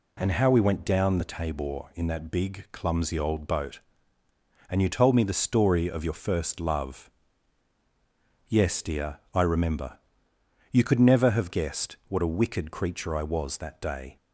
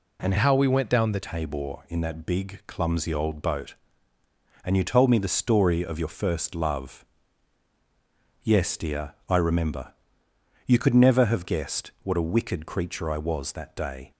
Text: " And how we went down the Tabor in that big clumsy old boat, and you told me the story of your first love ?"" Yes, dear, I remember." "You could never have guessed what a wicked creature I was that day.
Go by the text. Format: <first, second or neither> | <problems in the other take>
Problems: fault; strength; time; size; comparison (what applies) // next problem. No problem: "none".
first | changes voice from "how" to "the"; from 0.3 to 1.2 s; 0.9 s long